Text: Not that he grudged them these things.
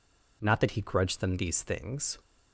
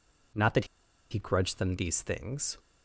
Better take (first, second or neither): first